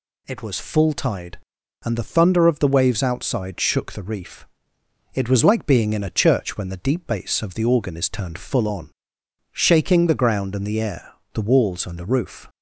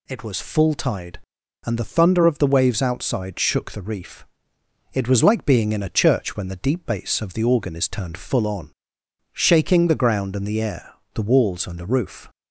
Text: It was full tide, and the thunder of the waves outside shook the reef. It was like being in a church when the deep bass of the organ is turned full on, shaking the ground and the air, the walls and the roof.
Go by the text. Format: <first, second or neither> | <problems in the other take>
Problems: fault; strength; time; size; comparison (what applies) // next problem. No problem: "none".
neither | none